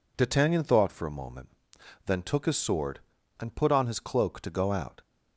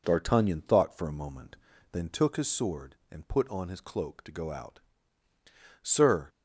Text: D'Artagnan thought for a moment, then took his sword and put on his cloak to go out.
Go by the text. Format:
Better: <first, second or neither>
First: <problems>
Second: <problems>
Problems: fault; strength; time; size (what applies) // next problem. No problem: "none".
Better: first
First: none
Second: goes on to say "Sir"; slight; from 5.8 s on; 0.48 s long